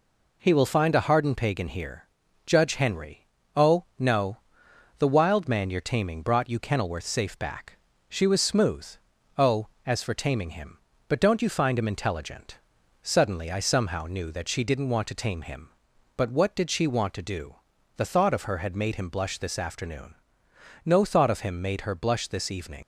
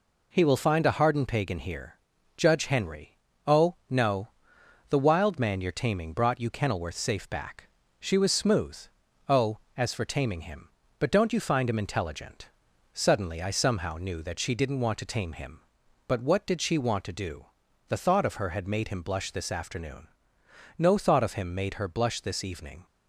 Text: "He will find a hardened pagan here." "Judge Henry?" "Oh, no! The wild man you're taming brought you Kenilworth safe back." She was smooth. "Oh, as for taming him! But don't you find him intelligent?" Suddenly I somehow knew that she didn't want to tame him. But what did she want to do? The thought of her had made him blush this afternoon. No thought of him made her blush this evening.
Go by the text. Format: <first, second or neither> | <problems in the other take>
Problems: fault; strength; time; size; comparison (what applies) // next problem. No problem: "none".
second | leaves "evening" unfinished; at 22.8 s; 90 ms